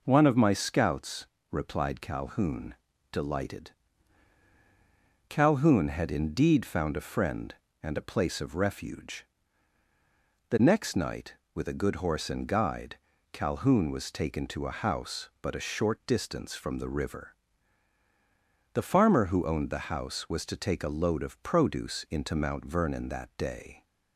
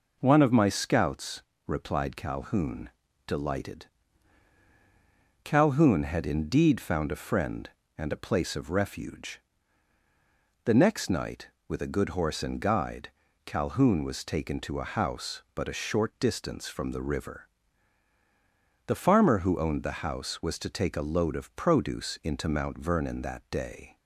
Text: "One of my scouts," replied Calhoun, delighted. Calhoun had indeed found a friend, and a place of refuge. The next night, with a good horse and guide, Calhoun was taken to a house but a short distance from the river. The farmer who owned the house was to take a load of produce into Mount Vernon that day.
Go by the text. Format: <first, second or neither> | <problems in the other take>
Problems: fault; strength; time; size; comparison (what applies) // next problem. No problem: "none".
neither | none